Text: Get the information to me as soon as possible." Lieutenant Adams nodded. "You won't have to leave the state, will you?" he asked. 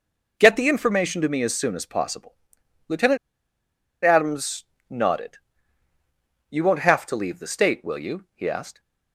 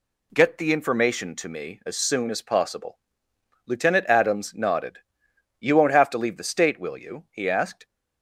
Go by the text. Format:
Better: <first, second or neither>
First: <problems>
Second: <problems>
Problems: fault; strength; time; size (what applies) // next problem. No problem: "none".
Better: second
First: pauses between "Lieutenant" and "Adams"; noticeable; at 3.1 s; 0.86 s long // pauses between "Adams" and "nodded"; slight; at 4.6 s; 0.26 s long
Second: none